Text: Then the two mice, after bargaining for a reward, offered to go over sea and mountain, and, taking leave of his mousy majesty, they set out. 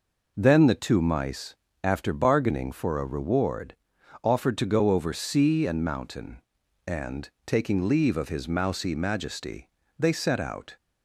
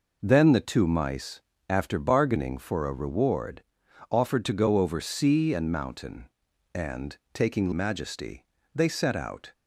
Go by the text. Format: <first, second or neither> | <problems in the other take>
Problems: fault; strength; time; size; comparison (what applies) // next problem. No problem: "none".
first | skips "leave of his mousy"; at 7.7 s